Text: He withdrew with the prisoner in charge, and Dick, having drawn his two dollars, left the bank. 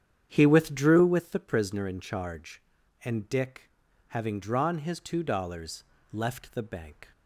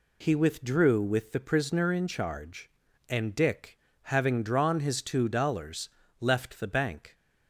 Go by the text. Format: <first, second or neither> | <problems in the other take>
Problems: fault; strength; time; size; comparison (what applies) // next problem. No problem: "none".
second | starts louder than the rest; strong; until 1.3 s; 9 dB